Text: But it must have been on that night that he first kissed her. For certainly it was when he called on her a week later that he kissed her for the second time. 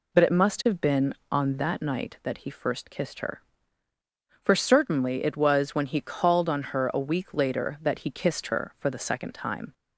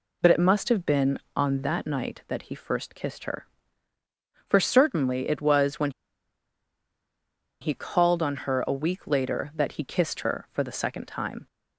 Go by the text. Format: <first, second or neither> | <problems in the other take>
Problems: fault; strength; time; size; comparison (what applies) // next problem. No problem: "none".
first | pauses between "when" and "he"; strong; at 5.8 s; 1.7 s long